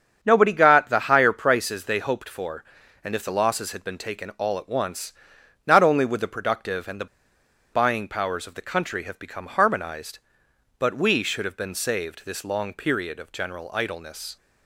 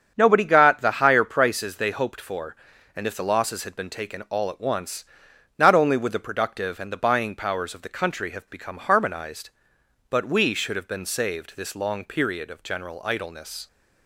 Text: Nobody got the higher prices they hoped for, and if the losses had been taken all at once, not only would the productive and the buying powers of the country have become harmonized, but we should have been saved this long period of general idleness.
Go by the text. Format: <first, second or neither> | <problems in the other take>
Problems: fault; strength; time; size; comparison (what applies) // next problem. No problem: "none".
second | starts louder than the rest; strong; until 1.2 s; 7.5 dB; strong in the second // pauses between "the" and "buying"; noticeable; at 7.0 s; 0.67 s long